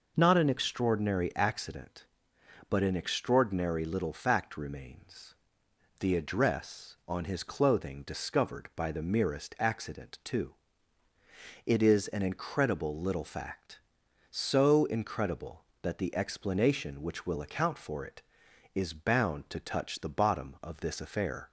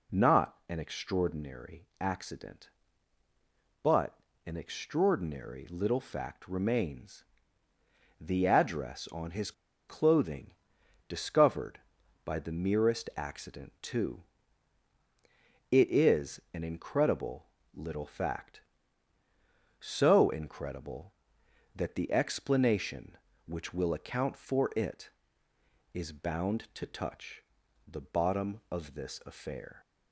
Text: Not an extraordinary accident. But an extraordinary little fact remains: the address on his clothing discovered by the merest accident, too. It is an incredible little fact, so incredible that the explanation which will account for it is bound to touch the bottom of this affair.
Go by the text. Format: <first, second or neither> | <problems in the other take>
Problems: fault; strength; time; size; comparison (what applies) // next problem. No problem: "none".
first | pauses between "But" and "an"; slight; at 4.1 s; 0.28 s long // pauses between "his" and "clothing"; at 9.5 s; 0.36 s long // pauses between "clothing" and "discovered"; noticeable; at 10.5 s; 0.56 s long // pauses between "incredible" and "little"; slight; at 17.4 s; 0.26 s long // pauses between "touch" and "the"; noticeable; at 27.4 s; 0.48 s long